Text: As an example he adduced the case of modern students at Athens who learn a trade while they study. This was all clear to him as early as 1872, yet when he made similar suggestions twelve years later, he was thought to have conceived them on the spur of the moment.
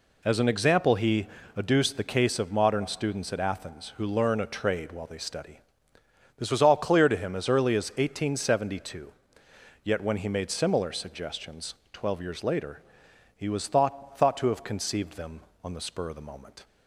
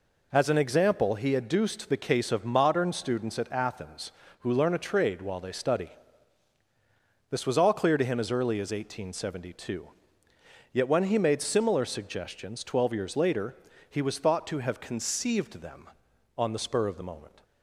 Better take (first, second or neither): second